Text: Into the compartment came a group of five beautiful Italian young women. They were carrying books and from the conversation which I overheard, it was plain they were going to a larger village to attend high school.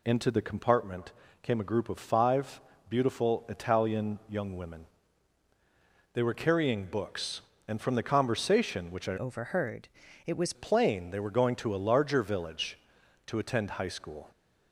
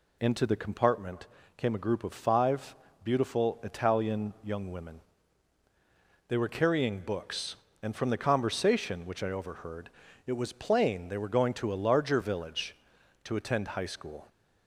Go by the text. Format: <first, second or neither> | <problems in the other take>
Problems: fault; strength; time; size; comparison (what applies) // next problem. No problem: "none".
second | pauses between "compartment" and "came"; slight; at 1.1 s; 0.30 s long; slight in the second // pauses between "five" and "beautiful"; slight; at 2.5 s; 0.30 s long; slight in the second // changes voice from "overheard" to "was"; from 9.1 to 10.5 s; 1.4 s long